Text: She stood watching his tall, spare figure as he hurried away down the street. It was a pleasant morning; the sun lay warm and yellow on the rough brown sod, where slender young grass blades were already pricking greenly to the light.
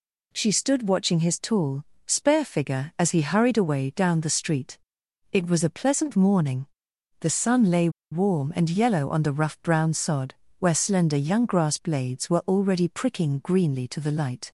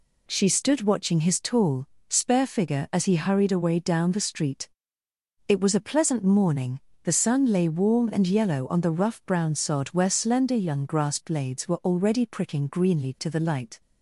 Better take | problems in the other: second | pauses between "lay" and "warm"; slight; at 7.8 s; 0.22 s long

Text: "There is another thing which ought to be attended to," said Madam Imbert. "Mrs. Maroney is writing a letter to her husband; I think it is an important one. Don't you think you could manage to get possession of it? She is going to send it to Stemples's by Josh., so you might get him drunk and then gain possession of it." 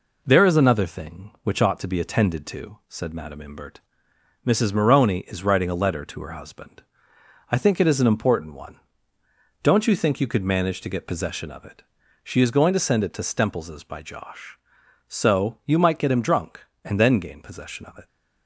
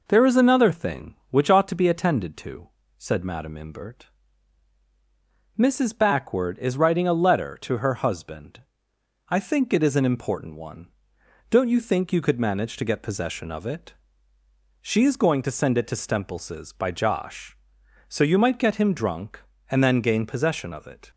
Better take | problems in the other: first | says "Backward" for "Maroney"; at 5.9 s

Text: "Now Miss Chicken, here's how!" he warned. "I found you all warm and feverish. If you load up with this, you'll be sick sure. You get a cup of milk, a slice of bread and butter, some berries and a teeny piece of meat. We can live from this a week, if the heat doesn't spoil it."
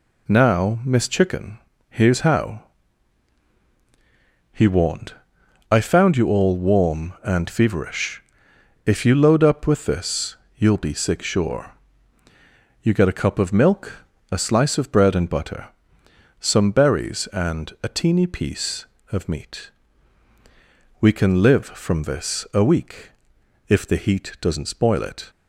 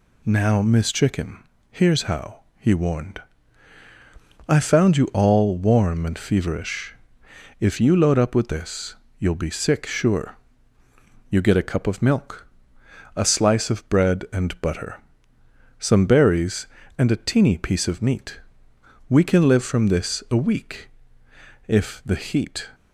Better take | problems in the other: first | stops before "doesn't spoil it"; at 22.7 s

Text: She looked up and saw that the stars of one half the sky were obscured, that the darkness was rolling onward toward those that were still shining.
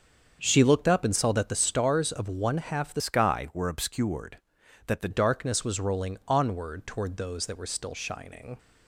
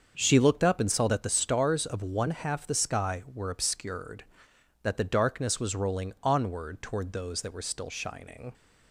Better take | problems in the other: second | starts louder than the rest; until 1.4 s; 7 dB; also in the second // changes voice from "sky" to "the"; from 3.0 to 5.0 s; 2.0 s long

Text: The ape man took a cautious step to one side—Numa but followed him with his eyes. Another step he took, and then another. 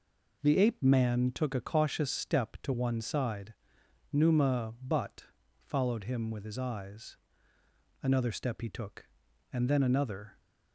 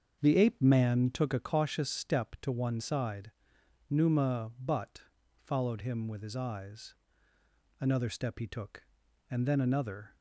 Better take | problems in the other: first | starts louder than the rest; until 1.5 s; 6.5 dB // pauses between "but" and "followed"; at 5.0 s; 0.42 s long; also in the first

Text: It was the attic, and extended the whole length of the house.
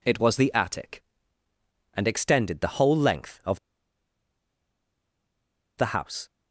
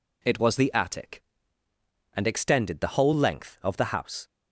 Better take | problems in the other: second | pauses between "of" and "the"; strong; at 3.5 s; 2.1 s long

